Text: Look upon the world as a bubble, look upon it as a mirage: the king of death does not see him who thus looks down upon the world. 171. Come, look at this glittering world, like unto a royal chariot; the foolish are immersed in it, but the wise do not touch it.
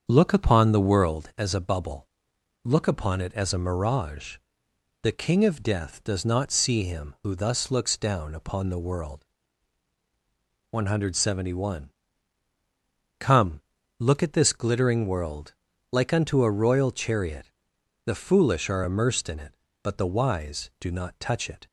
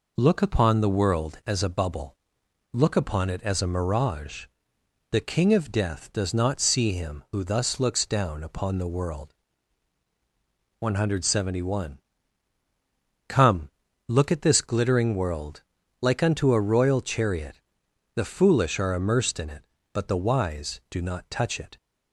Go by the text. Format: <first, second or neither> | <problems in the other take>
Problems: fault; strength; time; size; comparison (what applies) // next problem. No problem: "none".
second | starts louder than the rest; until 1.2 s; 7 dB